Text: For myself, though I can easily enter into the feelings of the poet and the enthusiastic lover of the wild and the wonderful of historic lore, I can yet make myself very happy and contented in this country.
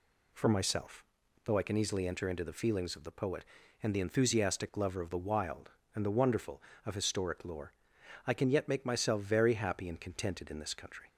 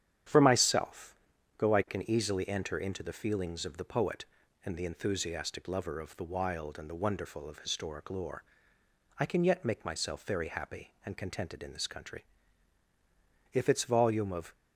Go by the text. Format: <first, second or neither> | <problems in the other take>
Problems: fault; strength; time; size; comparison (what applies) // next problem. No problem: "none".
first | starts louder than the rest; strong; until 1.7 s; 9.5 dB // goes on to say "If its volume of"; noticeable; from 13.5 s on; 1.0 s long